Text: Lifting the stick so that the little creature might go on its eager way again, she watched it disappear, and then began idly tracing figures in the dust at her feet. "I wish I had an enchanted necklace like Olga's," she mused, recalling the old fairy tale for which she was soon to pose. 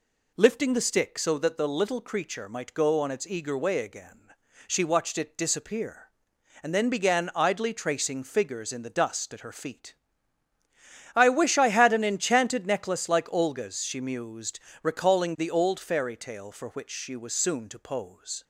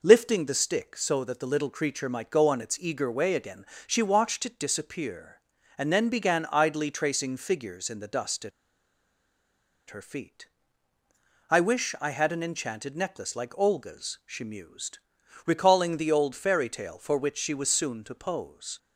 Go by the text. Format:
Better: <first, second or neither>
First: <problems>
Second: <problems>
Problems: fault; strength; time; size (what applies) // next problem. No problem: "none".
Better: first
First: none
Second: pauses between "at" and "her"; strong; at 8.5 s; 1.3 s long